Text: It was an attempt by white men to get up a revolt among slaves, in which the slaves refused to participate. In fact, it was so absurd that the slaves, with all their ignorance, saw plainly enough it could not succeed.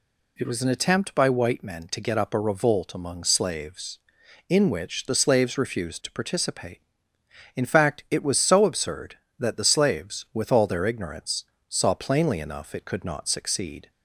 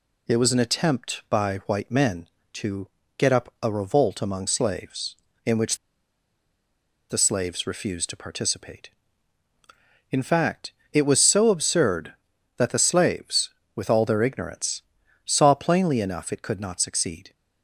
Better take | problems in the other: first | pauses between "to" and "get"; slight; at 2.8 s; 0.28 s long // pauses between "which" and "the"; strong; at 5.7 s; 1.3 s long

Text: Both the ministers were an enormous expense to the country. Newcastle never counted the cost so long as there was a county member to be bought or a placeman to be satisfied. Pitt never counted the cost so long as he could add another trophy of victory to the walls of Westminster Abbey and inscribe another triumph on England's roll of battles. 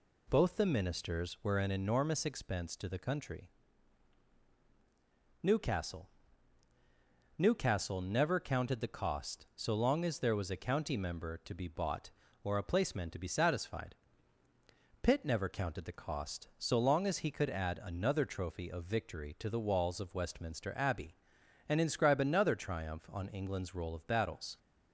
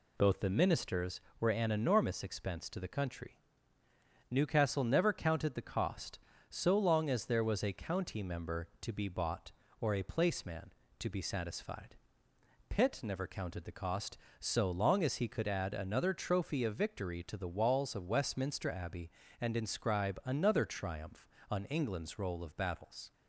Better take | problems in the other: second | says "Newcastle" twice; at 7.3 s

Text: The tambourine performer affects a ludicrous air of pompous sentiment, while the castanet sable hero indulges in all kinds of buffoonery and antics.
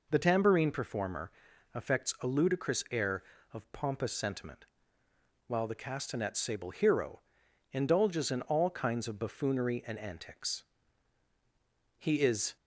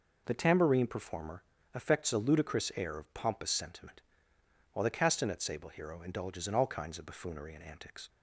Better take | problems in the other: second | pauses between "performer" and "affects"; at 1.3 s; 0.42 s long; slight in the second // pauses between "hero" and "indulges"; noticeable; at 7.1 s; 0.52 s long // goes on to say "He is"; from 11.9 s on; 0.58 s long

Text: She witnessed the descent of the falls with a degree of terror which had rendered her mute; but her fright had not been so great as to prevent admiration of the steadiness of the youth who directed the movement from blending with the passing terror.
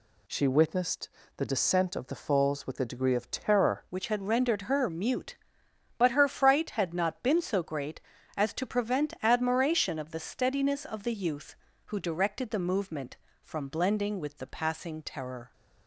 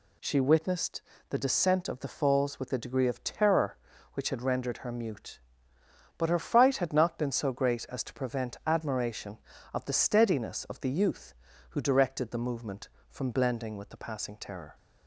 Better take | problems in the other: second | pauses between "witnessed" and "the"; slight; at 1.0 s; 0.30 s long; slight in the second // changes voice at "which"; from 3.9 s on; 11.6 s long

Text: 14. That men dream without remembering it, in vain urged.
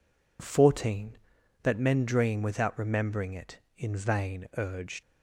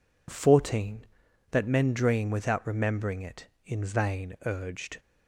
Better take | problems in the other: second | leaves "urged" unfinished; at 5.0 s; 80 ms

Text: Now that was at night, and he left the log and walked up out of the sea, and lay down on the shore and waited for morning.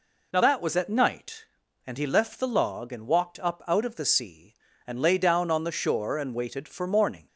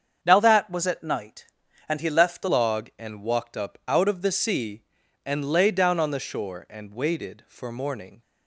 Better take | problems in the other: first | starts louder than the rest; strong; until 1.2 s; 7 dB // changes voice at "log"; from 2.4 s on; 5.8 s long

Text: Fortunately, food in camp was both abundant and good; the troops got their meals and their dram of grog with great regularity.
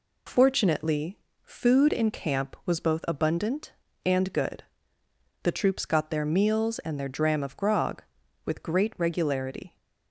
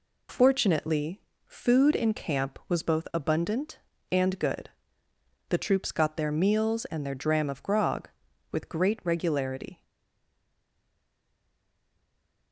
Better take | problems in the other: first | stays silent after the last word; strong; from 9.8 s on; 2.7 s long

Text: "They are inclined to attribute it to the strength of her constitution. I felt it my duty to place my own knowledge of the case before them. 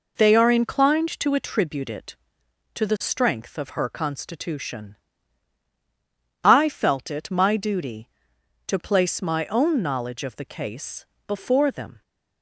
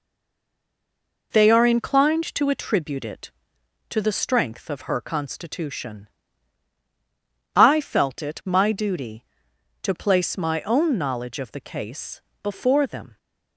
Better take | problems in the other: first | stays silent before the first word; noticeable; until 1.3 s; 1.3 s long // pauses between "case" and "before"; slight; at 12.2 s; 0.20 s long; slight in the first

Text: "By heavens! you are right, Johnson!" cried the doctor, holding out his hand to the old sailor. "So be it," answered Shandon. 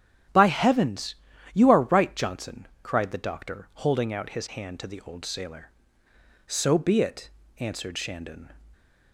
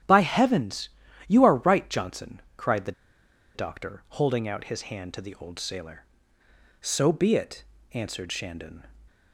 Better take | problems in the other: first | starts louder than the rest; strong; until 1.4 s; 10.5 dB; strong in the first // pauses between "the" and "doctor"; noticeable; at 2.9 s; 0.63 s long

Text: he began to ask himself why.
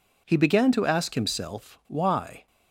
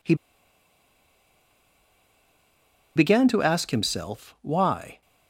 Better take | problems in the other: first | pauses between "he" and "began"; strong; at 0.1 s; 2.8 s long

